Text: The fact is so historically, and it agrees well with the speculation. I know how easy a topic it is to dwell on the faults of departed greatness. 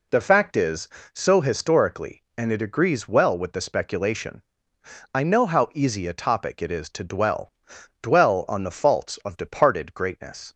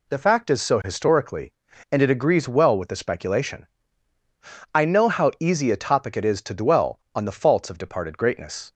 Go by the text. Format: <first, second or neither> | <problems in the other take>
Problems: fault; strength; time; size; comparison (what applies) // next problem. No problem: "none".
second | says "dwell" twice; at 8.0 s